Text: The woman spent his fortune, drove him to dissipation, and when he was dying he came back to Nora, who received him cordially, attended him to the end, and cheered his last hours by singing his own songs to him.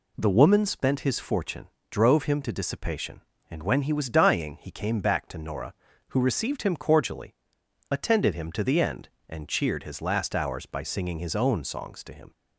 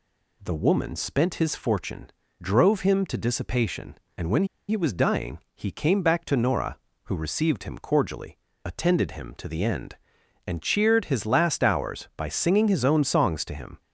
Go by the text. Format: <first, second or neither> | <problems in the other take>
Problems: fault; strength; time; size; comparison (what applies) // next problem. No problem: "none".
first | pauses between "when" and "he"; slight; at 4.4 s; 0.23 s long // pauses between "dying" and "he"; slight; at 5.3 s; 0.16 s long